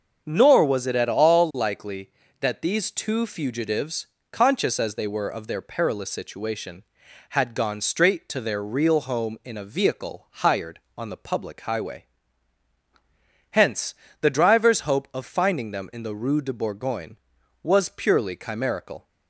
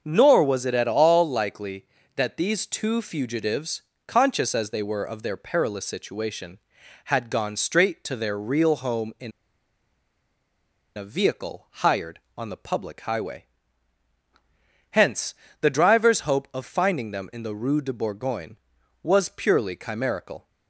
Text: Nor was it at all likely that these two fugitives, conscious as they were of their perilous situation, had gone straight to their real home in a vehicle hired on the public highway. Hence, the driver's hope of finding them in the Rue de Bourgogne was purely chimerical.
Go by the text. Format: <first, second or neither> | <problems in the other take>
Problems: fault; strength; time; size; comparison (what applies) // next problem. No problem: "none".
first | starts louder than the rest; until 1.0 s; 6.5 dB; also in the first // pauses between "in" and "a"; strong; at 9.3 s; 1.6 s long